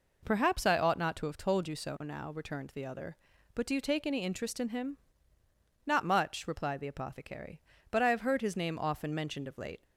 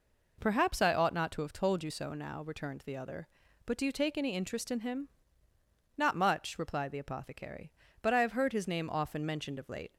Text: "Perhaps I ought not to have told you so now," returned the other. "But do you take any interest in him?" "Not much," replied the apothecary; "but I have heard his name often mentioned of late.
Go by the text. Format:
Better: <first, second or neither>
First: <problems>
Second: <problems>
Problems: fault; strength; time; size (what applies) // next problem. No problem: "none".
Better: neither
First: none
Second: none